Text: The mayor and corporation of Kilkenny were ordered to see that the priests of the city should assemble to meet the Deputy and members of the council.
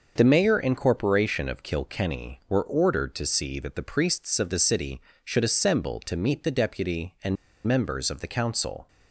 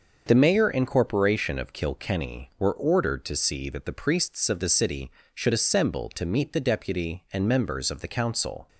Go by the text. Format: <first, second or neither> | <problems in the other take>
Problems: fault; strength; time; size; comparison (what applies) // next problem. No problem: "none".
second | starts louder than the rest; until 1.1 s; 6 dB; also in the second // pauses between "and" and "members"; slight; at 7.3 s; 0.31 s long